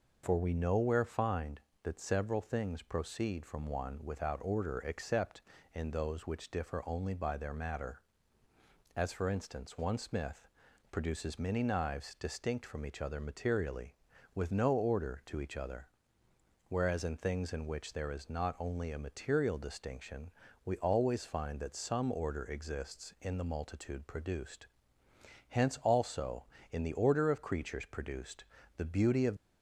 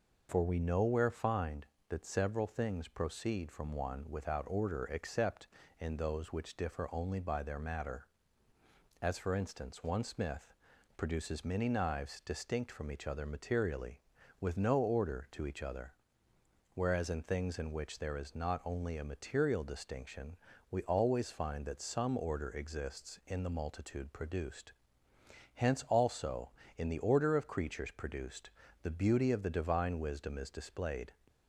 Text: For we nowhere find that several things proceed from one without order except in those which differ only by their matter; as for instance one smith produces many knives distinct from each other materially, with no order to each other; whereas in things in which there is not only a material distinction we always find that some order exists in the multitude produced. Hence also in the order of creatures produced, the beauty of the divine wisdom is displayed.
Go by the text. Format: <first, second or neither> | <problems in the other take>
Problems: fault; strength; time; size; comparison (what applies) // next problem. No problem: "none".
second | pauses between "smith" and "produces"; at 10.4 s; 0.44 s long; also in the second // pauses between "distinction" and "we"; slight; at 20.3 s; 0.34 s long; slight in the second // stops before "the divine wisdom is displayed"; at 29.3 s